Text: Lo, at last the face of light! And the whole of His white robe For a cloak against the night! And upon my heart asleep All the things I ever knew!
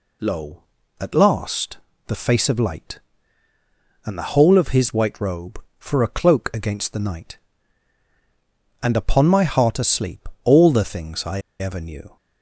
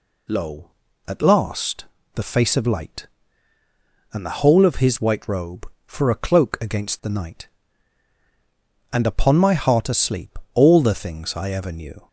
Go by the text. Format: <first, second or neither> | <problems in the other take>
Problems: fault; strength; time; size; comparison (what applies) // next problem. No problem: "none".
second | pauses between "last" and "the"; slight; at 1.7 s; 0.30 s long; slight in the second // pauses between "asleep" and "All"; slight; at 10.2 s; 0.18 s long; slight in the second // pauses between "I" and "ever"; slight; at 11.4 s; 0.18 s long